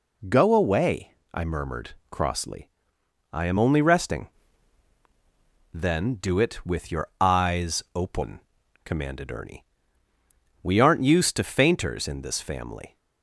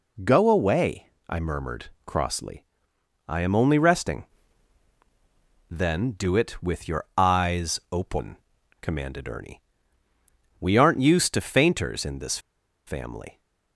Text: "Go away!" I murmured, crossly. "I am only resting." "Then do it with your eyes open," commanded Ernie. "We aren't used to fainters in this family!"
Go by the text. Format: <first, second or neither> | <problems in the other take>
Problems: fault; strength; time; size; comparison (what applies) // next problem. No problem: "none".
first | pauses between "this" and "family"; noticeable; at 12.3 s; 0.48 s long